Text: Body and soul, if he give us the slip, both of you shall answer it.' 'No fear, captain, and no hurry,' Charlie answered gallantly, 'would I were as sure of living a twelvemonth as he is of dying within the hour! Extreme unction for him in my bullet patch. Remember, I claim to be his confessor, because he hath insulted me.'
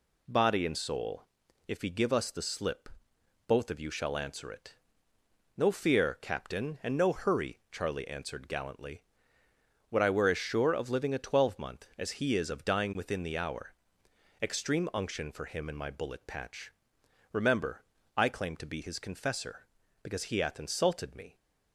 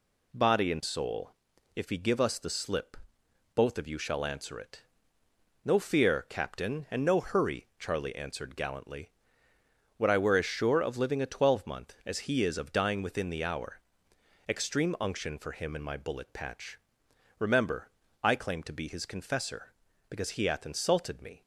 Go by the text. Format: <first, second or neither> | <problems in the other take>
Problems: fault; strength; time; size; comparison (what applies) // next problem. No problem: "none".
neither | none